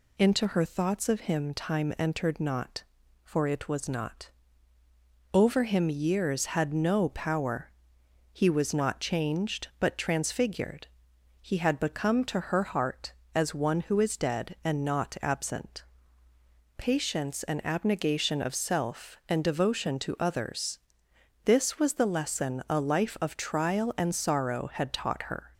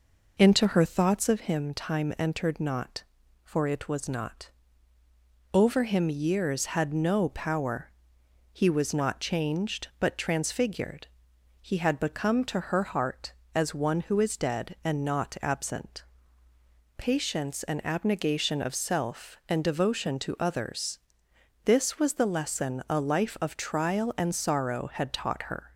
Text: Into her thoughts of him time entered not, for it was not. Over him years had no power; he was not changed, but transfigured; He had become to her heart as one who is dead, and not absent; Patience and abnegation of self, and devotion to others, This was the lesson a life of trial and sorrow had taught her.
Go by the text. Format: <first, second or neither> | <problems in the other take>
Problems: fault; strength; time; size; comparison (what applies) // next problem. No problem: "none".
first | starts louder than the rest; noticeable; until 1.4 s; 5 dB